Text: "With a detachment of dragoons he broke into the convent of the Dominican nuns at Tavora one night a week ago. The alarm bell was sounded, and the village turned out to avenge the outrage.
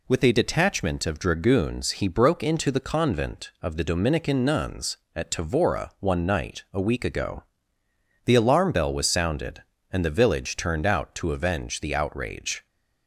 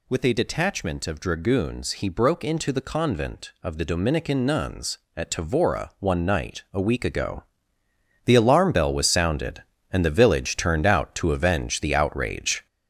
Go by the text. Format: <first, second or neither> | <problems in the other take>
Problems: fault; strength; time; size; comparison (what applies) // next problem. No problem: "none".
first | gets louder; noticeable; throughout; 5.5 dB